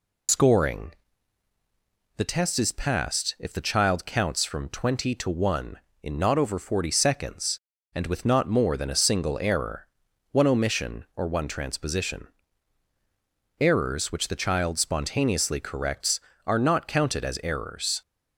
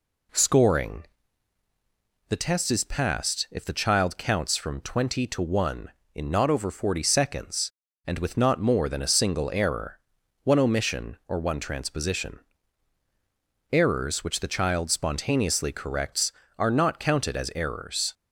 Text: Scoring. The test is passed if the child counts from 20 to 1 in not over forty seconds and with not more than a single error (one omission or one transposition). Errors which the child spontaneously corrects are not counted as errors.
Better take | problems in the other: second | loses the start of "Scoring"; at 0.2 s; 95 ms

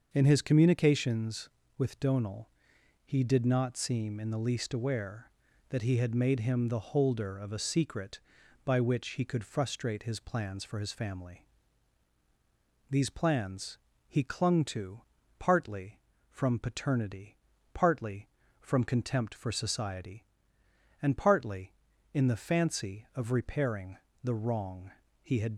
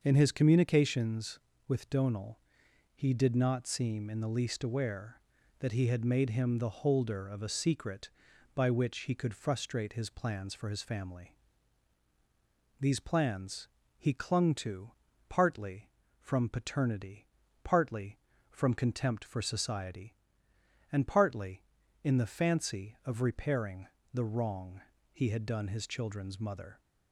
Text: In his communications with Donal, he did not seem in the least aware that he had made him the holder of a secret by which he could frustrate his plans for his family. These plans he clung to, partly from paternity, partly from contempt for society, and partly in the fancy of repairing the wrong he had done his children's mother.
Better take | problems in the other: second | starts louder than the rest; until 1.1 s; 6.5 dB; also in the second // pauses between "plans" and "he"; slight; at 13.7 s; 0.28 s long; slight in the second // pauses between "repairing" and "the"; slight; at 23.9 s; 0.26 s long; slight in the second // pauses between "wrong" and "he"; slight; at 24.9 s; 0.32 s long; slight in the second // stops before "done his children's mother"; at 25.5 s

